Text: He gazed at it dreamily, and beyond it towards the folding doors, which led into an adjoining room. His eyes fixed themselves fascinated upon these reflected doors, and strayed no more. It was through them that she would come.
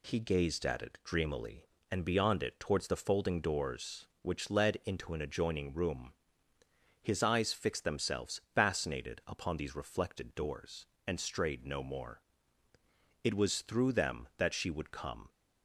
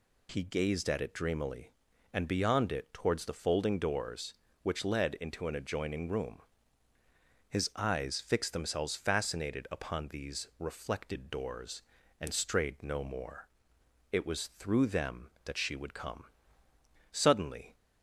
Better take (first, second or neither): first